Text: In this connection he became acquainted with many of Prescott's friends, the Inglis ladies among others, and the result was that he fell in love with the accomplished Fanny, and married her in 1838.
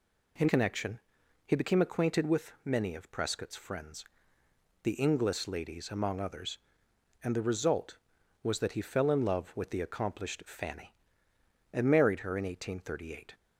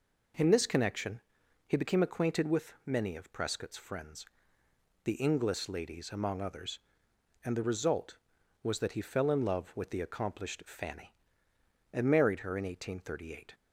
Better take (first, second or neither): second